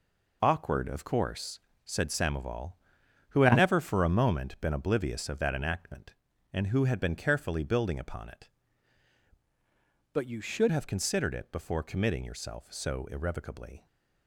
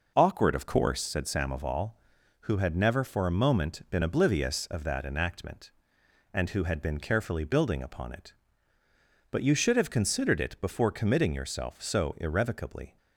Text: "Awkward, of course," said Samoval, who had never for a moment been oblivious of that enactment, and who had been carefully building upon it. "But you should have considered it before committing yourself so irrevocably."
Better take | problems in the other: second | changes voice from "But" to "should"; from 10.1 to 10.7 s; 0.6 s long

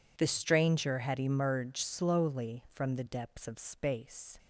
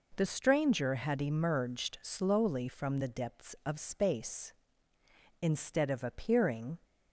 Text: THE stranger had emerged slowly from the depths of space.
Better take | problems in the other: first | goes on to say "Instead of appearing"; from 5.4 s on; 1.3 s long

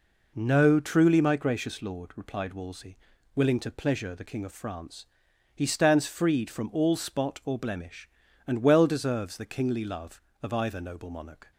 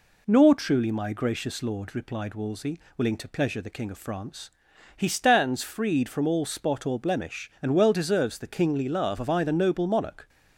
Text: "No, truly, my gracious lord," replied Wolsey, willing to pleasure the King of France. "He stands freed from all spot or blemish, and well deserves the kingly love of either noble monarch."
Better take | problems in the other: first | says "Nor" for "No"; at 0.2 s

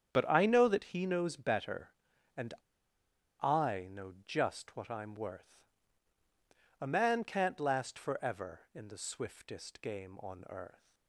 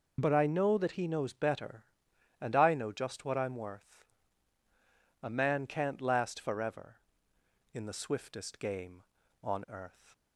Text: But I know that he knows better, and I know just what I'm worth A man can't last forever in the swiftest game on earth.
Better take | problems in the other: second | starts louder than the rest; strong; until 1.1 s; 8.5 dB // pauses between "and" and "I"; noticeable; at 2.5 s; 0.87 s long // pauses between "worth" and "A"; at 5.5 s; 1.2 s long; also in the second

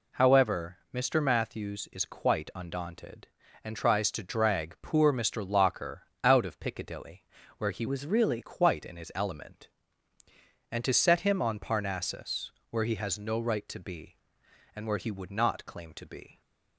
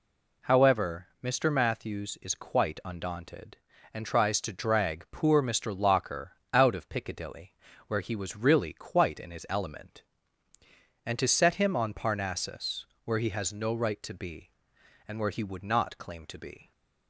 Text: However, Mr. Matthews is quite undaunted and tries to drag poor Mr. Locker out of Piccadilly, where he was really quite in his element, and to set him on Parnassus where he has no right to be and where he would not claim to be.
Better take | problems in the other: second | pauses between "Locker" and "out"; slight; at 6.0 s; 0.20 s long; slight in the second // changes voice from "was" to "really"; from 7.8 to 8.3 s; 0.5 s long // pauses between "Parnassus" and "where"; slight; at 12.5 s; 0.20 s long; slight in the second

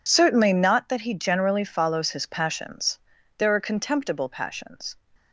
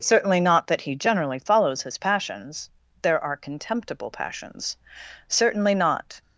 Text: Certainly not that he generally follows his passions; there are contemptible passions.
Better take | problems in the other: first | goes on to say "Certainly not"; noticeable; from 5.2 s on; 0.94 s long

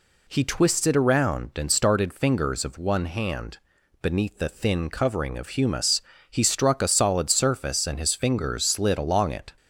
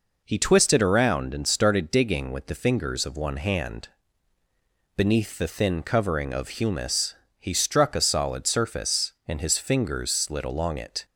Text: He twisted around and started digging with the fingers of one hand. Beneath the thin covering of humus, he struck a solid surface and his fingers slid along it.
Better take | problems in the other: second | skips "digging with the"; at 2.1 s

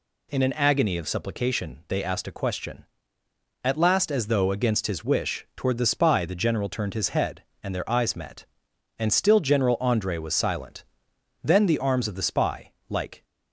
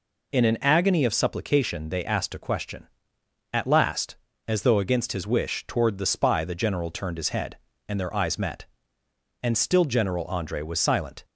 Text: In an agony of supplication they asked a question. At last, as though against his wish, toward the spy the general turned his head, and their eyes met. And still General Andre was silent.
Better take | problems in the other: second | goes on to say "Then the arms of the spy like"; strong; from 11.4 s on; 1.8 s long

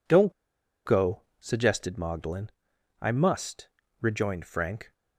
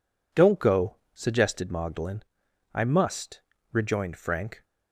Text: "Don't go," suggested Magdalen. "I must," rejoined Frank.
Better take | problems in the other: second | pauses between "Don't" and "go"; noticeable; at 0.3 s; 0.53 s long

